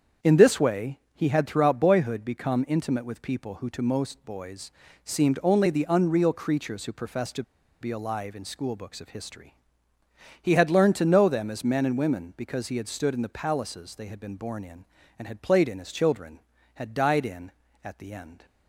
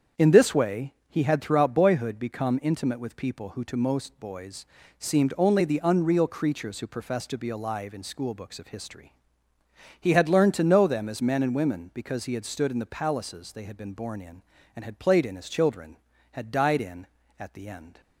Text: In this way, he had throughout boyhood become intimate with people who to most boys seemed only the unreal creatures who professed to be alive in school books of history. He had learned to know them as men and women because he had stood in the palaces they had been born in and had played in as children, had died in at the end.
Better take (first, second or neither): second